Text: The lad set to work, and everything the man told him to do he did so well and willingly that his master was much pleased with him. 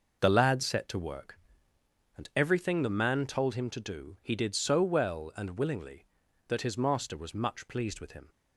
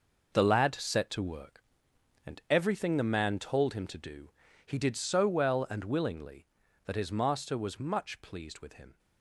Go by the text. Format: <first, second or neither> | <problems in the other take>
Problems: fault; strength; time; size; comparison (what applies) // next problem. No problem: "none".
first | gets quieter; strong; throughout; 10 dB // pauses between "do" and "he"; slight; at 4.3 s; 0.34 s long